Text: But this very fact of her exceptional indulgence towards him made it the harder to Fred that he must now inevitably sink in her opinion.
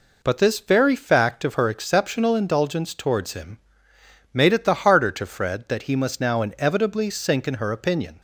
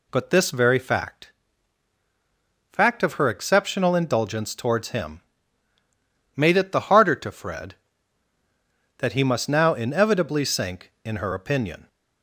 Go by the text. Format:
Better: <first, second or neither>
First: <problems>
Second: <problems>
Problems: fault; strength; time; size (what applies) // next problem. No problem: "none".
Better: first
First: pauses between "him" and "made"; noticeable; at 3.5 s; 0.74 s long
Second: says "fact" twice; at 2.7 s // pauses between "him" and "made"; at 5.1 s; 1.1 s long